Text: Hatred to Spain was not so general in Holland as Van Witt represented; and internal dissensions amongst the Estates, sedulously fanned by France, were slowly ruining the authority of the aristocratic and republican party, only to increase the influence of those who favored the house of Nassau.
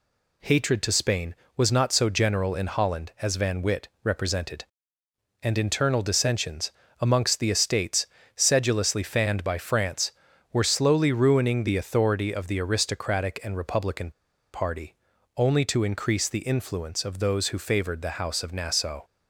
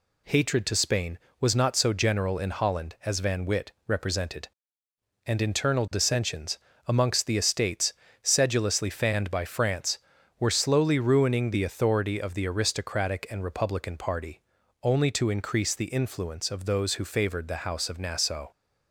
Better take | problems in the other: second | pauses between "Witt" and "represented"; slight; at 3.8 s; 0.16 s long; slight in the second // pauses between "dissensions" and "amongst"; slight; at 6.7 s; 0.26 s long; slight in the second // pauses between "republican" and "party"; at 14.0 s; 0.43 s long

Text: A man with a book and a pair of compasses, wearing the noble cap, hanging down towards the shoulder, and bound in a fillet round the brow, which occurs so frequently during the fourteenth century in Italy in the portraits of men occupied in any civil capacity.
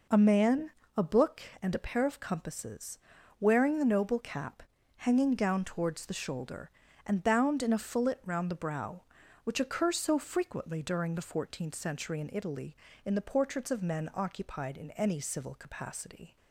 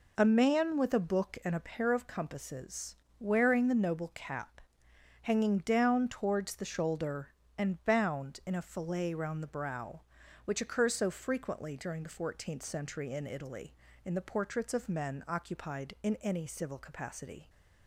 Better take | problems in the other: second | skips "with"; at 0.8 s

